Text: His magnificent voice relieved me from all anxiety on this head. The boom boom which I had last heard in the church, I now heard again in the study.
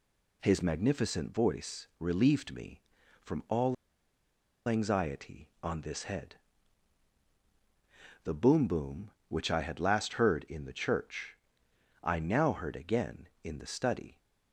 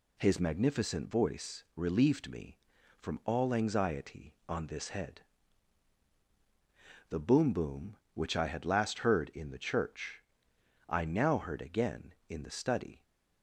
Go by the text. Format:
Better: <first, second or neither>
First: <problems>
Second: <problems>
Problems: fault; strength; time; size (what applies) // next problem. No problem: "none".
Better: second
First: pauses between "all" and "anxiety"; noticeable; at 3.7 s; 0.92 s long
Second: none